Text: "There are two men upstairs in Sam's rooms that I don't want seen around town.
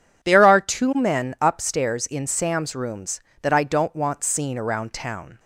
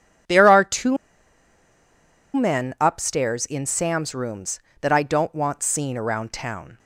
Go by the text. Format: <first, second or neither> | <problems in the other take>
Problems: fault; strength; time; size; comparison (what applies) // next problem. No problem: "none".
first | pauses between "two" and "men"; strong; at 0.9 s; 1.3 s long